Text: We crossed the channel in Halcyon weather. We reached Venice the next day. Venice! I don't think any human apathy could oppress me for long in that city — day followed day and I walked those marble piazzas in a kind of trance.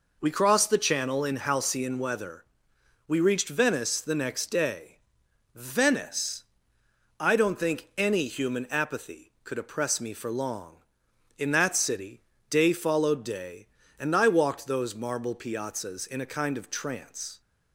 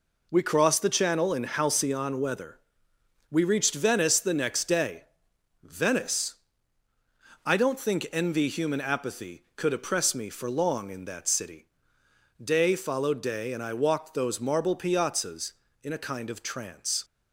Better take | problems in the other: first | says "envy" for "any"; at 8.1 s

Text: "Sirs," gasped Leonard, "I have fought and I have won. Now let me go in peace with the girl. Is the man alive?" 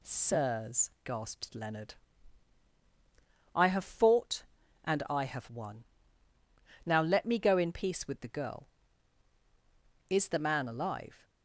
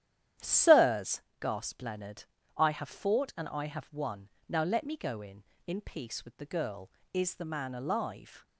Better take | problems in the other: first | starts louder than the rest; strong; until 1.6 s; 10.5 dB // says "in" twice; at 5.6 s

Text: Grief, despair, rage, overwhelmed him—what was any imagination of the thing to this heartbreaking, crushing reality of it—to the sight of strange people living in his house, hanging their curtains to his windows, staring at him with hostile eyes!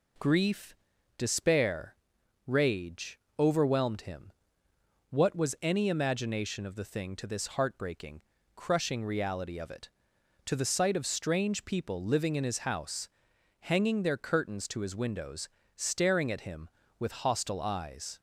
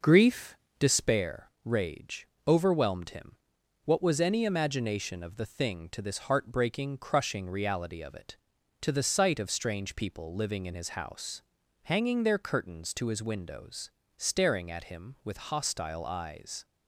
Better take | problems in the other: first | starts louder than the rest; noticeable; until 1.2 s; 5.5 dB

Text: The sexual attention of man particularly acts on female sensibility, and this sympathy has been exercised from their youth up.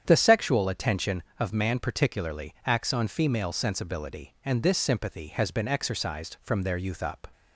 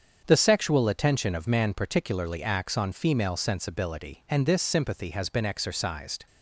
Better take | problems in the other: first | starts louder than the rest; strong; until 1.2 s; 7.5 dB; strong in the first // stops before "from their youth up"; at 6.2 s

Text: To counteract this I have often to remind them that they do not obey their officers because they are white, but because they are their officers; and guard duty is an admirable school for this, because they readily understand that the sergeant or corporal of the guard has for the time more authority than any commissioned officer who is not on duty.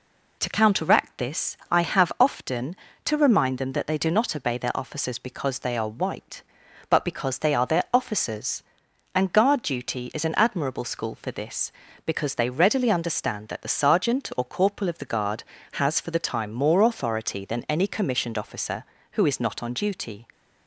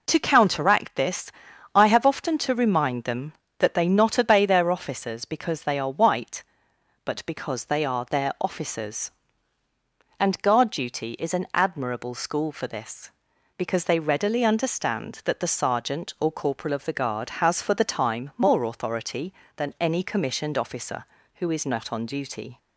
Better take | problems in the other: first | pauses between "this" and "I"; at 1.3 s; 0.42 s long // skips "do"; at 3.8 s

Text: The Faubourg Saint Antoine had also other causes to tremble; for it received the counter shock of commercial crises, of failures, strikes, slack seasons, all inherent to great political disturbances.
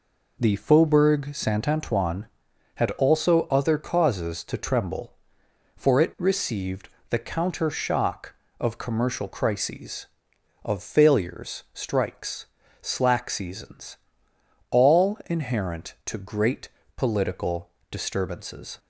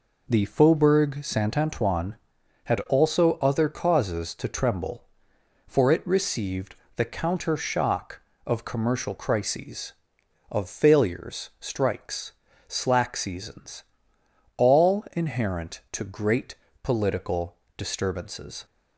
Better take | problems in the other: neither | pauses between "received" and "the"; slight; the same in both // pauses between "great" and "political"; slight; the same in both // pauses between "political" and "disturbances"; slight; the same in both

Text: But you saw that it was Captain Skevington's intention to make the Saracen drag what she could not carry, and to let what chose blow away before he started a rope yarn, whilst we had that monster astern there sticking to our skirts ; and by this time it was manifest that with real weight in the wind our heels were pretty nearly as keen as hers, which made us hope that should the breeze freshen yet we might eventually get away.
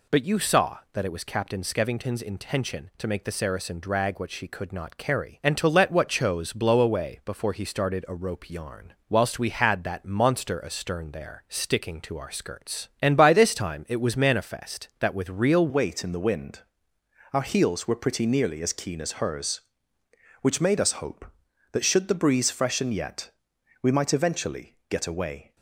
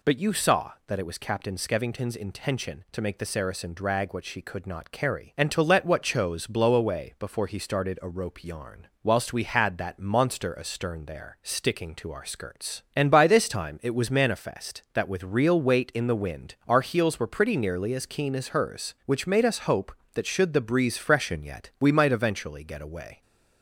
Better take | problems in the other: second | changes voice at "weight"; from 15.6 s on; 9.9 s long // pauses between "wind" and "our"; noticeable; at 16.5 s; 0.74 s long // pauses between "yet" and "we"; noticeable; at 23.3 s; 0.50 s long

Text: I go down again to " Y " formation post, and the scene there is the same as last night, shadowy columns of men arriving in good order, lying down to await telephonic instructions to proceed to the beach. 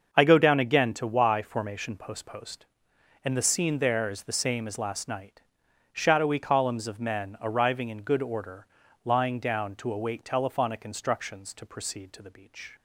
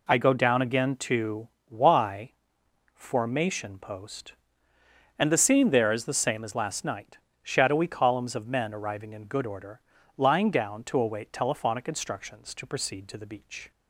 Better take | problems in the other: second | starts louder than the rest; until 1.1 s; 6.5 dB // says "post" twice; at 2.2 s

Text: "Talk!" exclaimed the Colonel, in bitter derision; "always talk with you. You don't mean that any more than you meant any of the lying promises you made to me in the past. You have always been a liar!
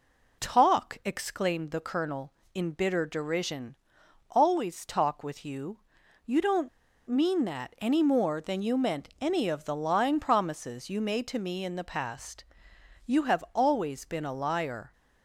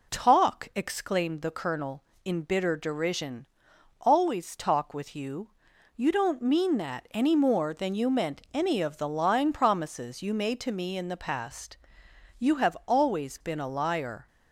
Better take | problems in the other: second | pauses between "don't" and "mean"; at 6.6 s; 0.38 s long

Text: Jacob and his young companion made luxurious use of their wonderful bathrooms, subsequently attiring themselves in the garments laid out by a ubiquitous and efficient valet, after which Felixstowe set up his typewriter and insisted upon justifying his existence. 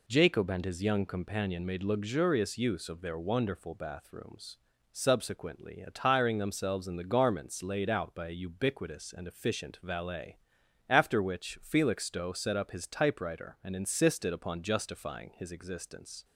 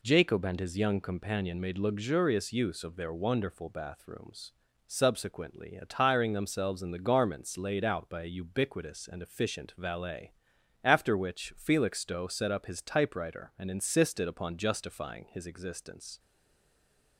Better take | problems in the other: first | stays silent after the last word; from 16.1 s on; 1.0 s long

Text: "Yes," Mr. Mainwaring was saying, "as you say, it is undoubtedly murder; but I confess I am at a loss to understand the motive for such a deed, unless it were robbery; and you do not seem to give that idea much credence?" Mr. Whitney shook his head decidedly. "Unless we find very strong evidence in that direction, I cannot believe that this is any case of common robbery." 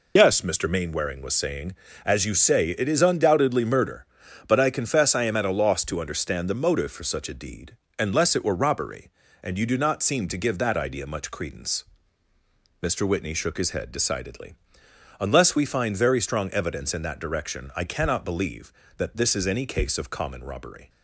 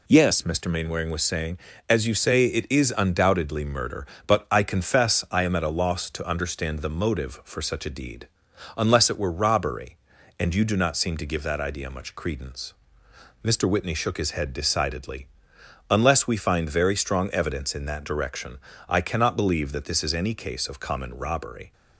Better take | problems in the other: second | loses the start of "Yes"; at 0.1 s; 65 ms

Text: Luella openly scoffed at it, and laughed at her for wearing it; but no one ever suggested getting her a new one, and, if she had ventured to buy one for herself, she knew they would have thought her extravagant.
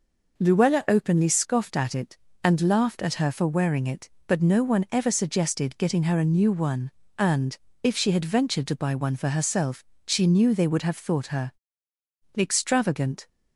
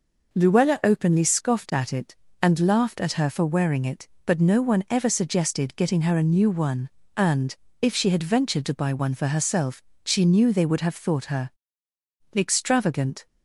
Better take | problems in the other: neither | pauses between "her" and "extravagant"; noticeable; the same in both

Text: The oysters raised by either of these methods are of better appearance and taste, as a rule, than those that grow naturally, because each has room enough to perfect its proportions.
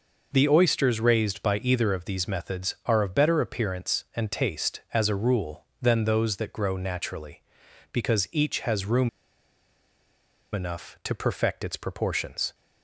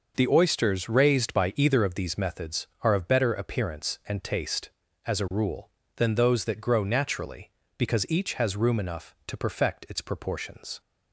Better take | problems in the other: second | pauses between "room" and "enough"; strong; at 9.0 s; 1.4 s long

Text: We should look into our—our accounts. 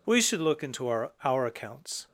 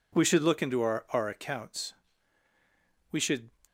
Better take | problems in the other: first | goes on to say "We should"; slight; from 3.1 s on; 0.38 s long

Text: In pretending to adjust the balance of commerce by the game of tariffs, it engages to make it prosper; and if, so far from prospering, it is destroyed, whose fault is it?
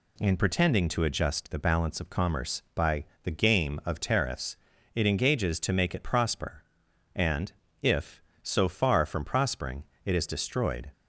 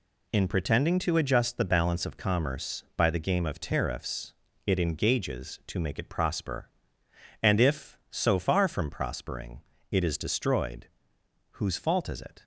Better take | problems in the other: second | pauses between "by" and "the"; slight; at 3.0 s; 0.18 s long // pauses between "and" and "if"; slight; at 7.5 s; 0.30 s long // stops before "whose fault is it"; at 10.9 s

